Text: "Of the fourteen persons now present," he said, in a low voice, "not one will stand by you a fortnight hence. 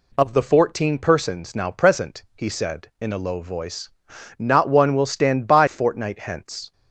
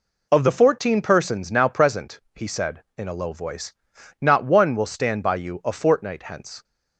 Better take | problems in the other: second | skips "you a"; at 5.6 s

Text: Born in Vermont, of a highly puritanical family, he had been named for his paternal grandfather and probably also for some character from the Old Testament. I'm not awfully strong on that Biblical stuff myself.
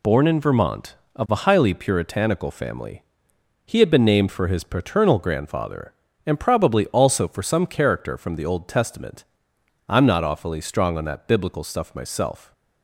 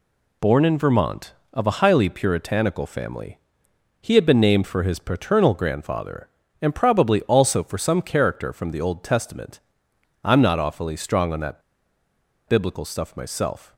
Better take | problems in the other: first | pauses between "that" and "Biblical"; noticeable; at 11.6 s; 0.88 s long

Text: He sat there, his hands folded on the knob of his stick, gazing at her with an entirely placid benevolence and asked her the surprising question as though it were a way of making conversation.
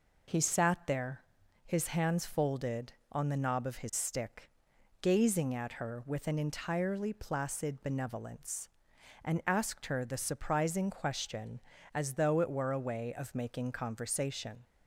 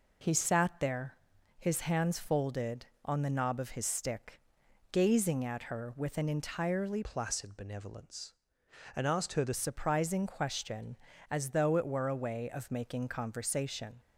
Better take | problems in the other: first | changes voice from "placid" to "the"; from 7.0 to 9.5 s; 2.5 s long

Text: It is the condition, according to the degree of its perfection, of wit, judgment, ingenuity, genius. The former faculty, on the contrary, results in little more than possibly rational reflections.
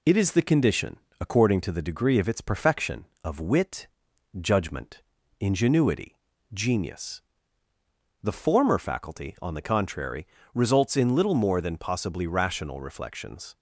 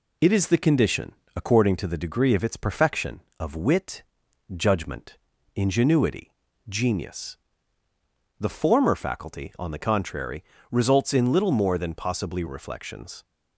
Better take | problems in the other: first | skips "rational"; at 12.4 s

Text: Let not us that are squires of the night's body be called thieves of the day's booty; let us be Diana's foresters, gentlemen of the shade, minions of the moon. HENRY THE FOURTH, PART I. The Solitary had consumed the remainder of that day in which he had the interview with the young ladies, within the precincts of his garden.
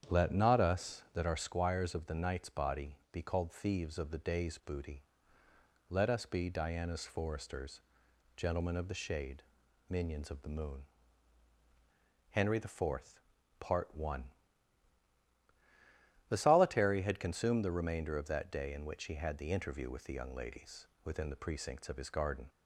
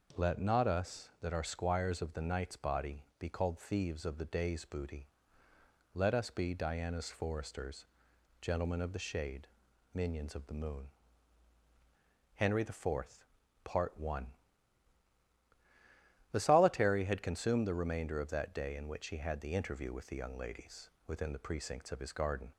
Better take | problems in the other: second | starts louder than the rest; strong; until 1.5 s; 9 dB

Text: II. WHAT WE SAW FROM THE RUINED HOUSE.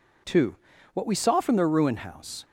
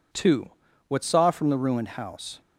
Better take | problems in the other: first | skips "WE"; at 1.0 s

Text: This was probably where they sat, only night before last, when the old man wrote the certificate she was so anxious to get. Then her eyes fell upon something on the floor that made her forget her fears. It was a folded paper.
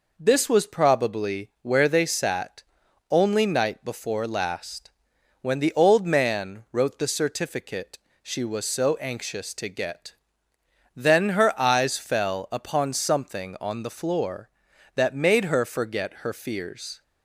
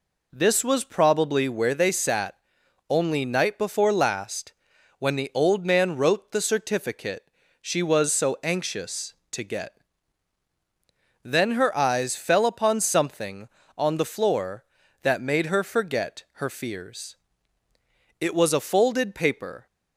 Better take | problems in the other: second | pauses between "certificate" and "she"; slight; at 7.9 s; 0.24 s long; slight in the second // stops before "It was a folded paper"; at 17.0 s

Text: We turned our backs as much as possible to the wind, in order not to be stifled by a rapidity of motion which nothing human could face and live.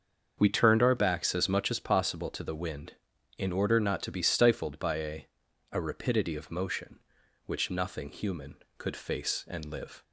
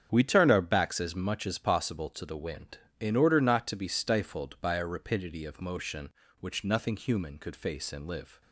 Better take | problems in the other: second | starts louder than the rest; until 1.3 s; 6.5 dB; strong in the second // says "a" twice; at 5.7 s

